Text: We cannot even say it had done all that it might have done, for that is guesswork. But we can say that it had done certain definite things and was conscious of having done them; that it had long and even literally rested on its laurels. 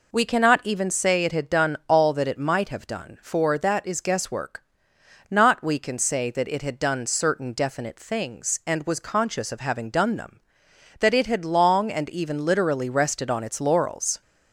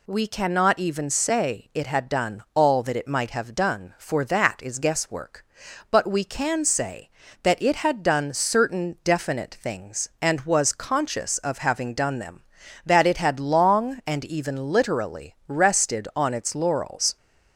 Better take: second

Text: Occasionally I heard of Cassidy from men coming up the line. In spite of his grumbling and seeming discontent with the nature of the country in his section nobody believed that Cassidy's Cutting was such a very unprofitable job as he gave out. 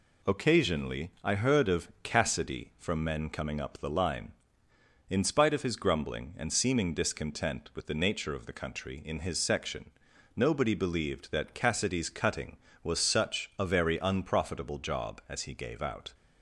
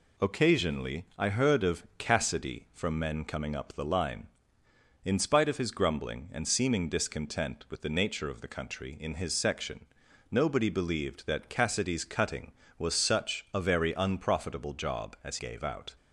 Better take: first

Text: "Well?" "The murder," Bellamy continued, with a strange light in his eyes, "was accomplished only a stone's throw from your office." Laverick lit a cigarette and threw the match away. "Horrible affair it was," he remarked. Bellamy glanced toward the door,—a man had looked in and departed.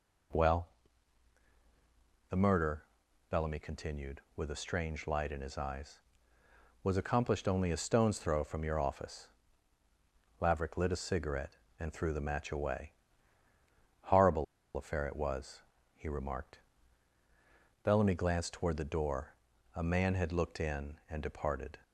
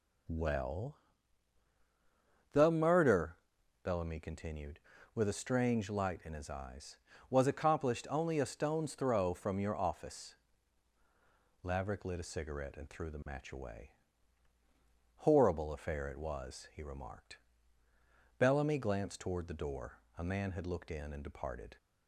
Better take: second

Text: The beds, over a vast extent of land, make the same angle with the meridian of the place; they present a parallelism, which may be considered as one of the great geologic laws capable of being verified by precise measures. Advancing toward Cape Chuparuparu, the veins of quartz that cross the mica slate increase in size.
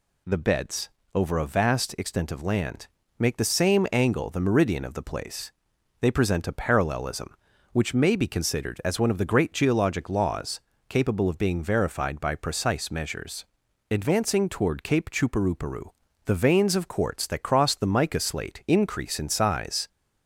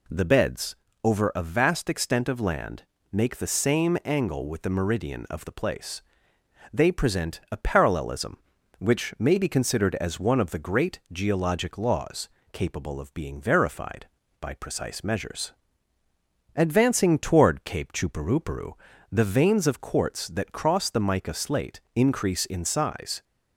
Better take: second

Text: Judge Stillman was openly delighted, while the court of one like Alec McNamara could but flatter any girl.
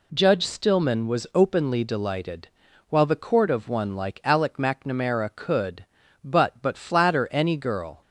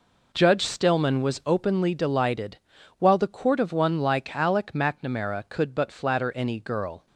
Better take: second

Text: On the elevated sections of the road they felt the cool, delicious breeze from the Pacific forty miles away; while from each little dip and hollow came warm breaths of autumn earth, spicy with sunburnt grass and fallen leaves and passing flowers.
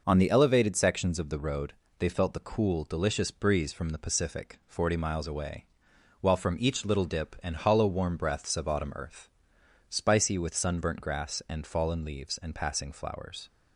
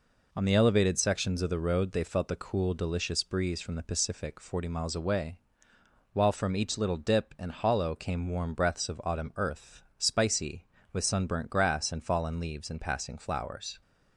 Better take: second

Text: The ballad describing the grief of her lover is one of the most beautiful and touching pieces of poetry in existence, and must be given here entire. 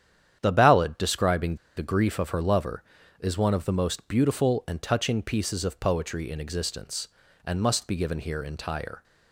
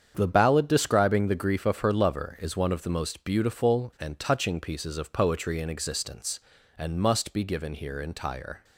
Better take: second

